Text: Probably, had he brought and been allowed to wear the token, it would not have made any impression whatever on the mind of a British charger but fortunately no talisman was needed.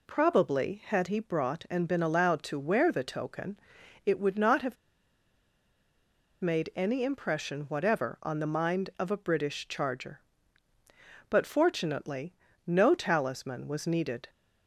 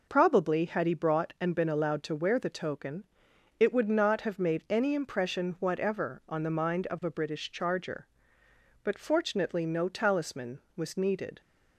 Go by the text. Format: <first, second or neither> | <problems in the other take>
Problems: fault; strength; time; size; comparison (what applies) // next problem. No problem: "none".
second | pauses between "have" and "made"; strong; at 4.7 s; 1.6 s long // pauses between "fortunately" and "no"; slight; at 12.3 s; 0.32 s long